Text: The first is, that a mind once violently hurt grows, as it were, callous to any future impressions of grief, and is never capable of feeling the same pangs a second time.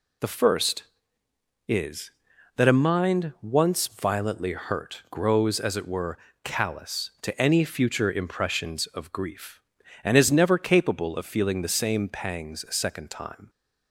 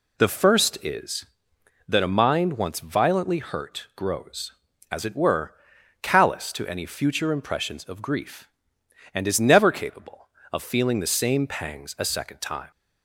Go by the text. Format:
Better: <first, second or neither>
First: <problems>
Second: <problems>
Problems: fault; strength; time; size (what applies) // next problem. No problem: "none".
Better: neither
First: none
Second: none